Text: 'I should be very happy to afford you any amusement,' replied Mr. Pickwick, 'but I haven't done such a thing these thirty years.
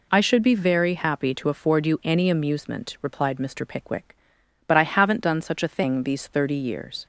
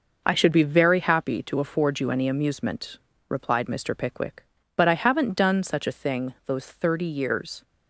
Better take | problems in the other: first | says "those" for "these"; at 6.4 s

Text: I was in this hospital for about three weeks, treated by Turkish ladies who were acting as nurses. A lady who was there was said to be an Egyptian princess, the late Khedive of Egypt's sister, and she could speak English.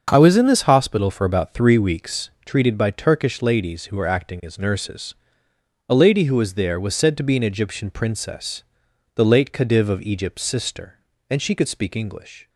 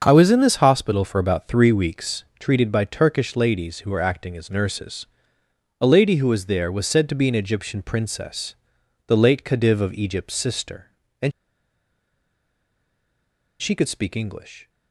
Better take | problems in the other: first | starts louder than the rest; until 1.0 s; 7 dB; also in the first // pauses between "and" and "she"; strong; at 11.3 s; 2.2 s long

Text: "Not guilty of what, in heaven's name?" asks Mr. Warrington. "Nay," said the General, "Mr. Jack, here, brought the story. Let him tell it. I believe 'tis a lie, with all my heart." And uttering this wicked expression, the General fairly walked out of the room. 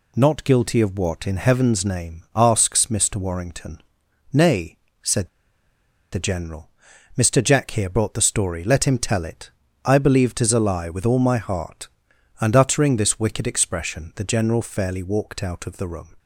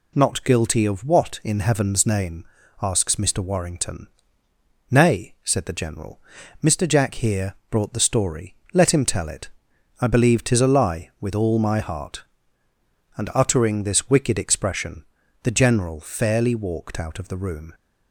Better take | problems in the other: second | pauses between "said" and "the"; noticeable; at 5.2 s; 0.83 s long

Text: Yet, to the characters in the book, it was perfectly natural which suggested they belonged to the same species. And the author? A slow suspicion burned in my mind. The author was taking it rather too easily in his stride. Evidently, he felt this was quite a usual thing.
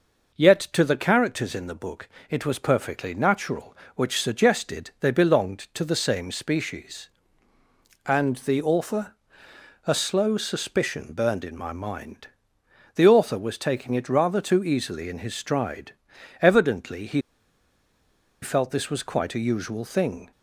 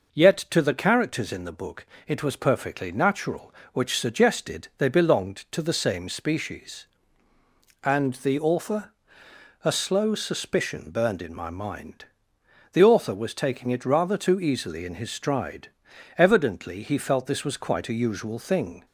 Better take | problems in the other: second | pauses between "he" and "felt"; at 17.2 s; 1.2 s long

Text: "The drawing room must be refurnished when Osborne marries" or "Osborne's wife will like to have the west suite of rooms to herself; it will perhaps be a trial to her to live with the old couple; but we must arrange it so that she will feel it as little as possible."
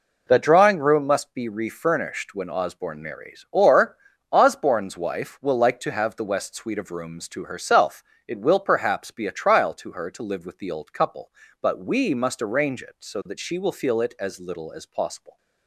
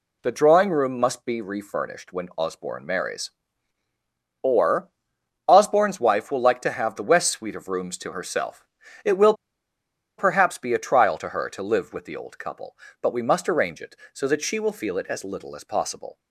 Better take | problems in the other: first | pauses between "or" and "Osborne's"; noticeable; at 4.9 s; 0.56 s long; slight in the first // pauses between "will" and "perhaps"; noticeable; at 9.3 s; 0.85 s long

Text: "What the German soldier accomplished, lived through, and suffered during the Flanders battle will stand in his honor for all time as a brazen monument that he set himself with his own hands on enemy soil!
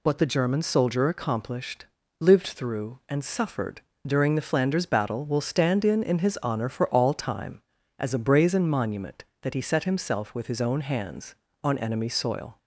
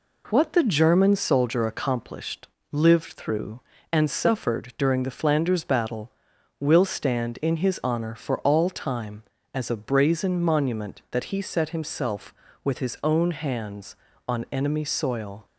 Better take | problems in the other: second | pauses between "suffered" and "during"; slight; at 3.8 s; 0.24 s long // says "in" twice; at 6.0 s

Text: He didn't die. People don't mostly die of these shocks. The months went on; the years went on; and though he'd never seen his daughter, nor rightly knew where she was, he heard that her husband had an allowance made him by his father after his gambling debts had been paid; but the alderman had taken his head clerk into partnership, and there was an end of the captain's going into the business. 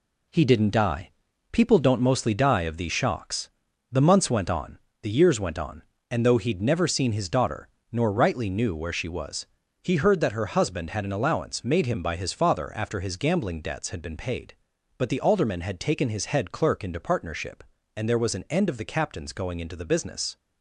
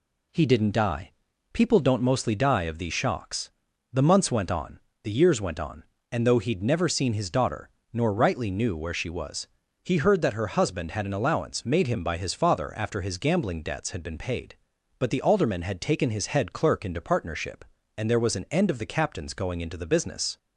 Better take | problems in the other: second | gets quieter; throughout; 6.5 dB

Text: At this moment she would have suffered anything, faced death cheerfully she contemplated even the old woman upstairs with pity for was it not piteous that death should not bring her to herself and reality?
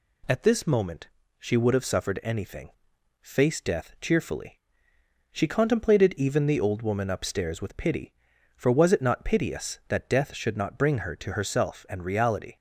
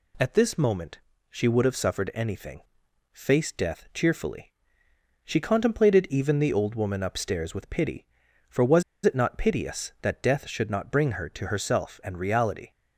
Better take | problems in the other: first | pauses between "moment" and "she"; slight; at 0.9 s; 0.30 s long; slight in the first // pauses between "cheerfully" and "she"; noticeable; at 4.5 s; 0.76 s long; noticeable in the first // pauses between "was" and "it"; slight; at 8.8 s; 0.23 s long

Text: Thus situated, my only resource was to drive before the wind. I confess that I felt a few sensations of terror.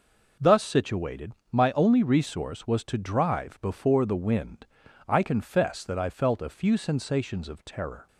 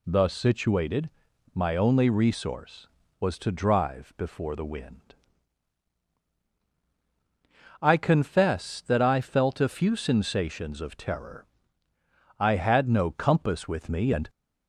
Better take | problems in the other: first | goes on to say "I had no compass with me and"; strong; from 12.3 s on; 1.9 s long

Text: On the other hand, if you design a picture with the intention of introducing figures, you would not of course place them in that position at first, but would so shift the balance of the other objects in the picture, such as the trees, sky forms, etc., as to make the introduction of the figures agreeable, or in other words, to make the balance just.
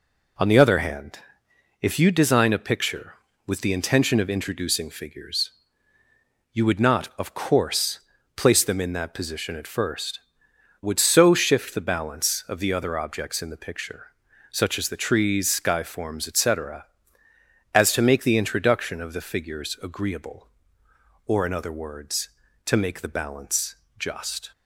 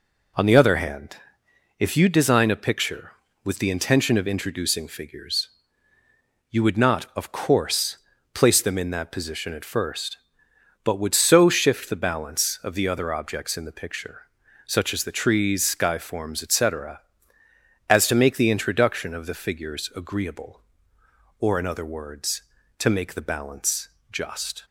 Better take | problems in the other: second | pauses between "course" and "place"; slight; at 8.0 s; 0.34 s long; slight in the second // skips "but"; at 10.5 s // pauses between "balance" and "just"; slight; at 23.7 s; 0.22 s long; slight in the second

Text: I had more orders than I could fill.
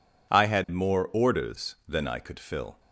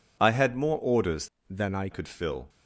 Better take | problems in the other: first | changes voice from "than" to "I"; from 1.4 to 1.8 s; 0.4 s long

